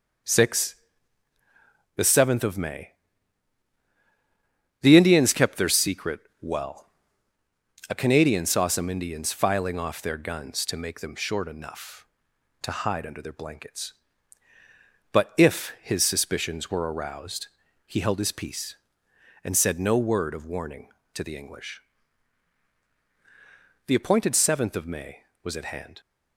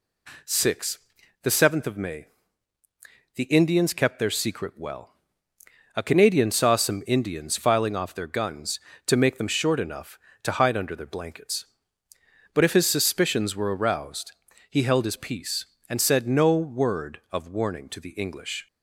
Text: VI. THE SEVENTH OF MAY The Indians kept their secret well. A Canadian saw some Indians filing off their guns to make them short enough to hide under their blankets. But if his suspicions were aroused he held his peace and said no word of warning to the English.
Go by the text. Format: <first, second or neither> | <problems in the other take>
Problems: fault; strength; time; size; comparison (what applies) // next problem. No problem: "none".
second | pauses between "MAY" and "The"; strong; at 2.9 s; 1.8 s long; also in the second // pauses between "secret" and "well"; slight; at 6.2 s; 0.20 s long // pauses between "aroused" and "he"; at 17.4 s; 0.38 s long; slight in the second // goes on to say "The appointed seventh of May was at hand"; strong; from 23.8 s on; 2.1 s long